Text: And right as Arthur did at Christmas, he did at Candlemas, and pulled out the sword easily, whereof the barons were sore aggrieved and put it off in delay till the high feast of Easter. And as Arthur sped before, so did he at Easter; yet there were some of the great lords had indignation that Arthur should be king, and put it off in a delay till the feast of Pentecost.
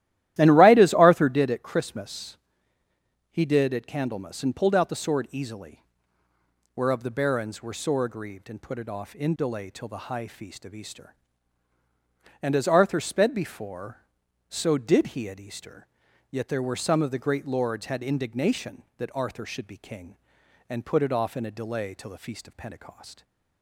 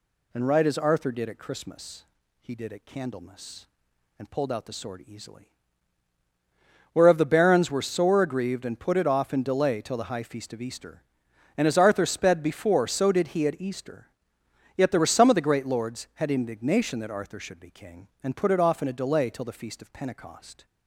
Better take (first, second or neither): second